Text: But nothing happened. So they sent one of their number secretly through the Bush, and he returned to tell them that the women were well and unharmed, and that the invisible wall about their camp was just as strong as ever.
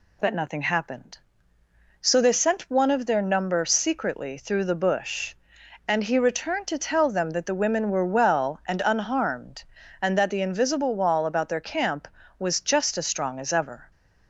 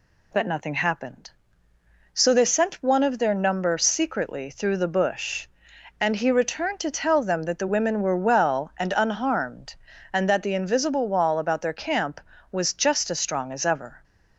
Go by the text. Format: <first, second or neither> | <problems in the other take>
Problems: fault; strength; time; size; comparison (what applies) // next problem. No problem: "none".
neither | none